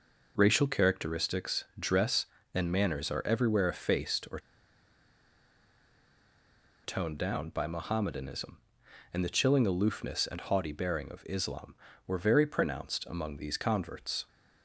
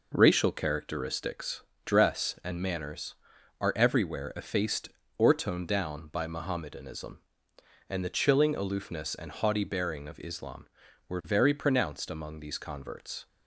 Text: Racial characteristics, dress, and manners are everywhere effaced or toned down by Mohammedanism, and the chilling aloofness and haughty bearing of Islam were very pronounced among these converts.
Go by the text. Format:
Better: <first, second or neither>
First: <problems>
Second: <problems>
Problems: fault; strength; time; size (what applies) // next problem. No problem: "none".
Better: second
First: pauses between "or" and "toned"; strong; at 4.3 s; 2.4 s long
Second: none